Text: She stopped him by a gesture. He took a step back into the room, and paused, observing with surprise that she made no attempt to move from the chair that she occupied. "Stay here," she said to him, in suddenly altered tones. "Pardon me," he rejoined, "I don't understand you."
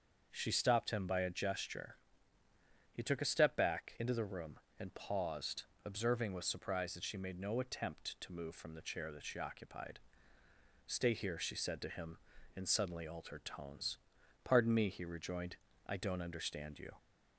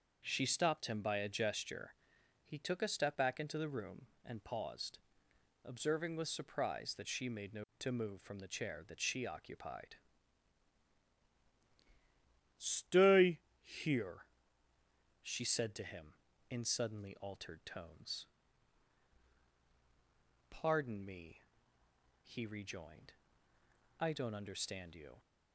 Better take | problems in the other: first | starts louder than the rest; until 1.2 s; 6 dB; also in the first // skips "attempt"; at 7.7 s // pauses between "Stay" and "here"; slight; at 13.4 s; 0.18 s long

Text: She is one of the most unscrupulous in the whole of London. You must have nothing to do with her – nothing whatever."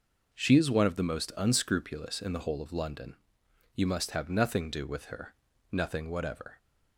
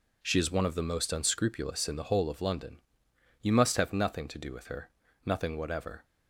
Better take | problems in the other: second | skips "to"; at 4.6 s

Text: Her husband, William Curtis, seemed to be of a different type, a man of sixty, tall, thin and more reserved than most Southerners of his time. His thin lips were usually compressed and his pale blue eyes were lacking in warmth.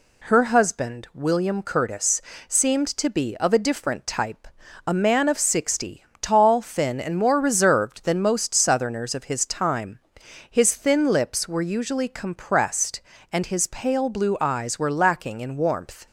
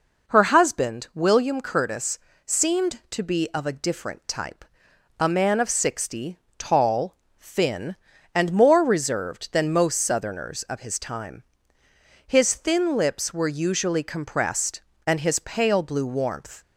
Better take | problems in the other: first | skips "eyes were lacking in"; at 16.0 s

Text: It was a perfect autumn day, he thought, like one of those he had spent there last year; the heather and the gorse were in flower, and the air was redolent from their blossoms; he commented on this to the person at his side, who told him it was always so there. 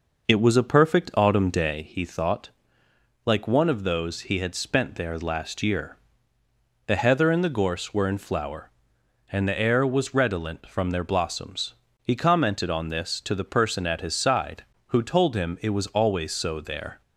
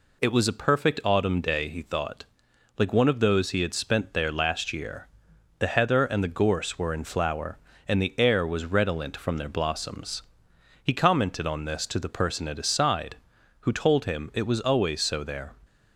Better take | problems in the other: second | starts louder than the rest; noticeable; until 1.9 s; 5.5 dB

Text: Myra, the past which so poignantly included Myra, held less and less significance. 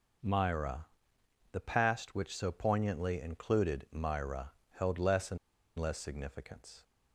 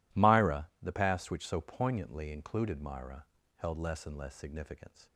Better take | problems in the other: second | pauses between "and" and "less"; at 5.3 s; 0.41 s long

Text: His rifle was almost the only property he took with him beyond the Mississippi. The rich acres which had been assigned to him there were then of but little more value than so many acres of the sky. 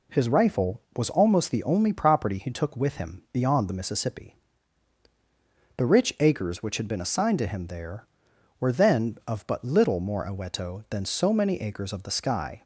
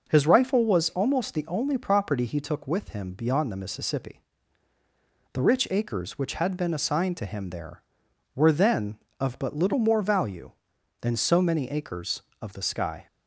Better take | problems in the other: second | says "aweto" for "value"; at 10.2 s

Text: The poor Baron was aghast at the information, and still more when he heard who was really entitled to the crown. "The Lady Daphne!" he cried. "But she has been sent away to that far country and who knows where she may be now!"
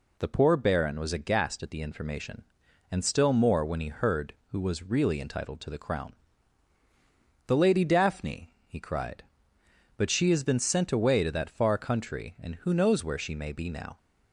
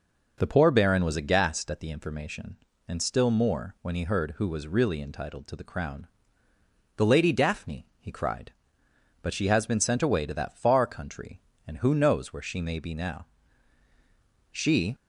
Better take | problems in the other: first | goes on to say "She"; slight; from 14.5 s on; 0.42 s long

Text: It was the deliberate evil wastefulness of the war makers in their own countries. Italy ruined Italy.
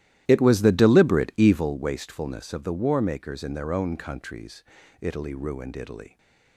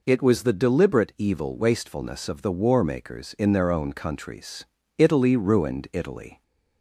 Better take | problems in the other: second | starts louder than the rest; strong; until 1.8 s; 14 dB

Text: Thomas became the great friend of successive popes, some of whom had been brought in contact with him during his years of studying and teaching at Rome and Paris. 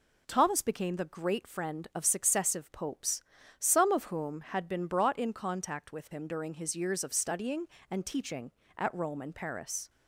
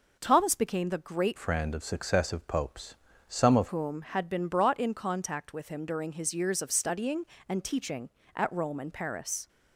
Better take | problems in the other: first | changes voice from "friend" to "of"; from 1.3 to 3.6 s; 2.3 s long

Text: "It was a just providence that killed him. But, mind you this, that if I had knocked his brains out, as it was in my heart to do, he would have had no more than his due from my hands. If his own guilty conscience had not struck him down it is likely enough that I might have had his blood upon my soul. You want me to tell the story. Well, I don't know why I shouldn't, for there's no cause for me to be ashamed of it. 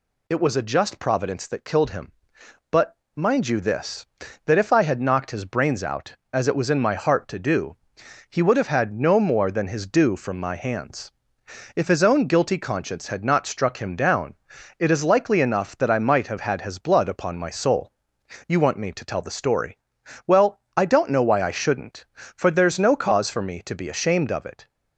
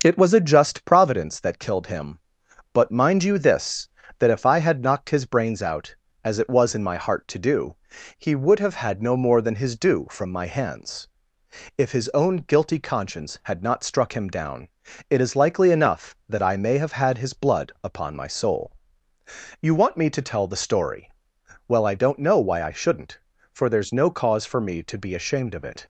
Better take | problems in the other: first | starts louder than the rest; until 1.0 s; 6.5 dB // pauses between "down" and "it"; at 14.6 s; 0.42 s long; also in the first // says "may" for "might"; at 16.5 s

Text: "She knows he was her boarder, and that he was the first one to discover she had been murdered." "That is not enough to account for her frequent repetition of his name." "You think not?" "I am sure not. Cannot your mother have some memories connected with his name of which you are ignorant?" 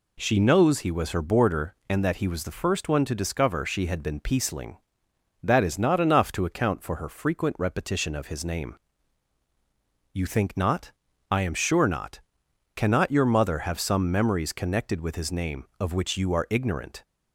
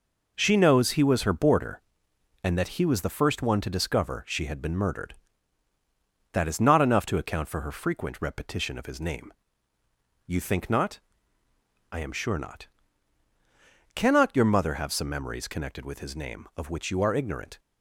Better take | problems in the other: second | says "peaceling" for "murdered"; at 4.1 s

